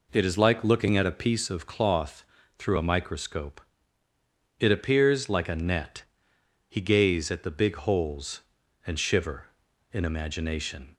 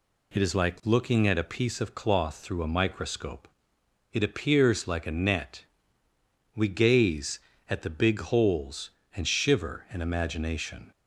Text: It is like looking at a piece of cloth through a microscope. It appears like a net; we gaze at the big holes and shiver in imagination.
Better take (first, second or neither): second